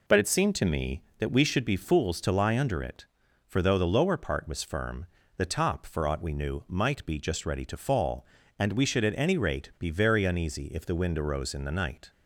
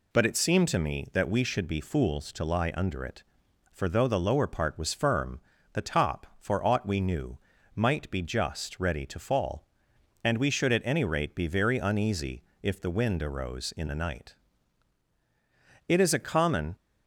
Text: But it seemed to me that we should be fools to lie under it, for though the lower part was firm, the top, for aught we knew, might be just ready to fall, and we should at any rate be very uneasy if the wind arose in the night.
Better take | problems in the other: first | pauses between "uneasy" and "if"; slight; at 12.4 s; 0.20 s long // goes on to say "It is a common"; noticeable; from 15.8 s on; 0.86 s long

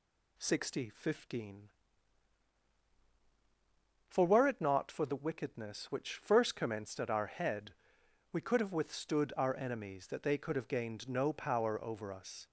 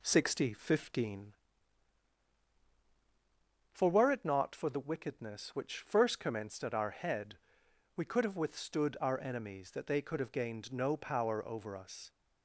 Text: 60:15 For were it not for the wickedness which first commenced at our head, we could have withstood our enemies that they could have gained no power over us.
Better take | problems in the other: first | starts louder than the rest; slight; until 1.4 s; 2.5 dB

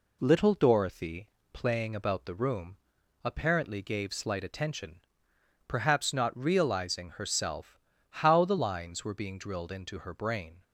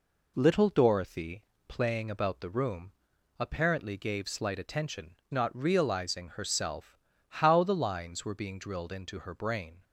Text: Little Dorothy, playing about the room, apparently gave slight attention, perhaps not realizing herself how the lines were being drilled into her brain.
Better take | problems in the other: first | skips "perhaps"; at 5.2 s // pauses between "herself" and "how"; slight; at 6.9 s; 0.30 s long; slight in the first

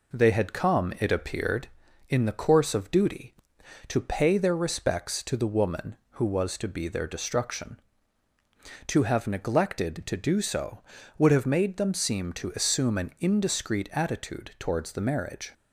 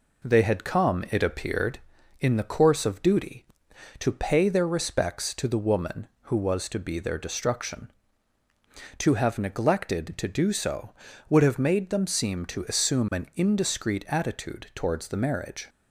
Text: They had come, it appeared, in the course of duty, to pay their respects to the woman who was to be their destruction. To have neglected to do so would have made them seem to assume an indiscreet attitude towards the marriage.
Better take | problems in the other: neither | none

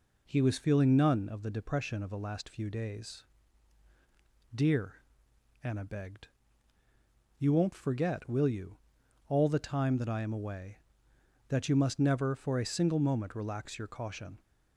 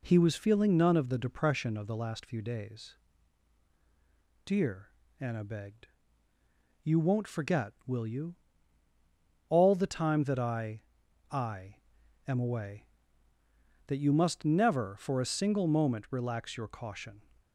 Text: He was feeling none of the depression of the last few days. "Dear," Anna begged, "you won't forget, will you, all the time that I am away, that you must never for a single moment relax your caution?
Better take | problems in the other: first | says "I" twice; at 11.2 s

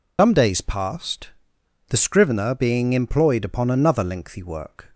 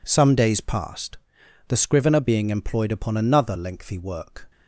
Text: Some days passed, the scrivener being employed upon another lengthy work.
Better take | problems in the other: second | loses the start of "Some"; at 0.1 s; 140 ms

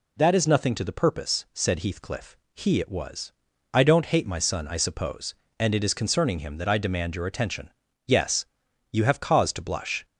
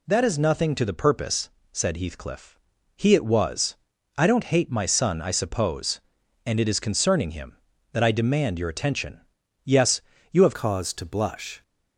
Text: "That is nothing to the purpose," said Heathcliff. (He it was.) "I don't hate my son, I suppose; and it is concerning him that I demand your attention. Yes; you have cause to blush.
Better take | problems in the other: first | changes voice at "cause"; from 10.5 s on; 1.1 s long

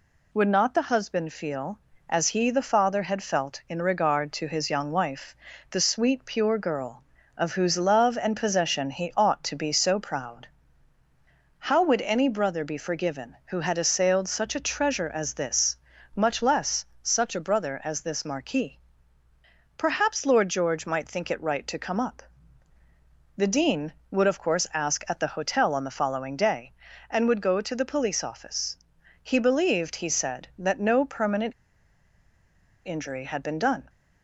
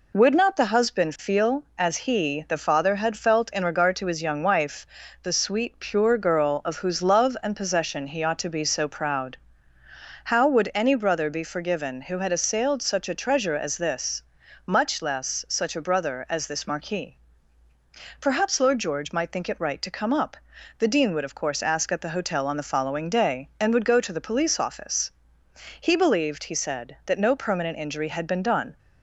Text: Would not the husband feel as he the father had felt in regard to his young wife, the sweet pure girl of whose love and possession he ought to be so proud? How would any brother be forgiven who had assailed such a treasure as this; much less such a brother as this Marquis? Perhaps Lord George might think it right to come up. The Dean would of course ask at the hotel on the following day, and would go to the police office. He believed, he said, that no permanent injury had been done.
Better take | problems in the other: second | pauses between "less" and "such"; slight; at 16.8 s; 0.18 s long // pauses between "permanent" and "injury"; strong; at 31.5 s; 1.3 s long

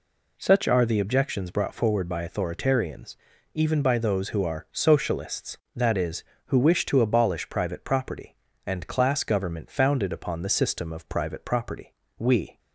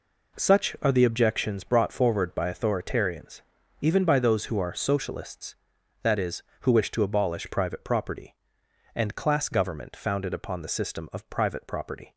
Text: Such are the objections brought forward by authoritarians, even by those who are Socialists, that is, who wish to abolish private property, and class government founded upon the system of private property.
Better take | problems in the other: second | goes on to say "We"; slight; from 12.1 s on; 0.40 s long

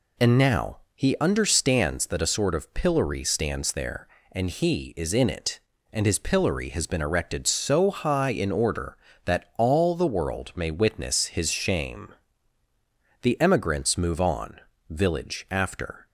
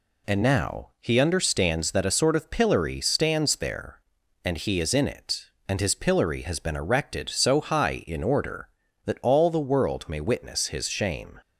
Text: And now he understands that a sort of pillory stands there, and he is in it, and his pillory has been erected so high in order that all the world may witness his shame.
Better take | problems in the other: second | pauses between "now" and "he"; slight; at 0.7 s; 0.16 s long // goes on to say "The emigrants move on village after"; strong; from 13.2 s on; 2.8 s long

